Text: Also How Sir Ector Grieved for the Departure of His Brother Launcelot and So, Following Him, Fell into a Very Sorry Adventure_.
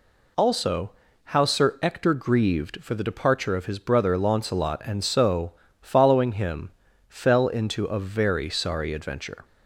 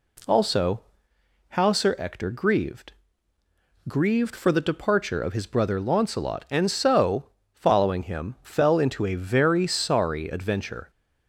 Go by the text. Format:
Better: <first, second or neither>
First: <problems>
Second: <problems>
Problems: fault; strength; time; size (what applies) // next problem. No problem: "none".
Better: first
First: pauses between "Also" and "How"; slight; at 0.9 s; 0.34 s long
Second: pauses between "Also" and "How"; noticeable; at 0.8 s; 0.70 s long // says "Grieved" twice; at 3.8 s